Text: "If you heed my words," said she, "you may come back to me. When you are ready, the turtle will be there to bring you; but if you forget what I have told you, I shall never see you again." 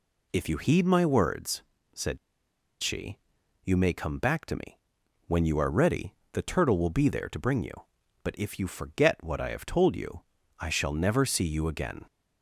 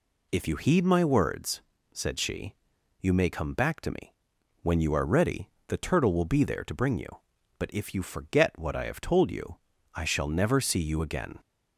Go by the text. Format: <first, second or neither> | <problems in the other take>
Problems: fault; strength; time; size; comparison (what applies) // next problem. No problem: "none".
second | pauses between "said" and "she"; noticeable; at 2.1 s; 0.64 s long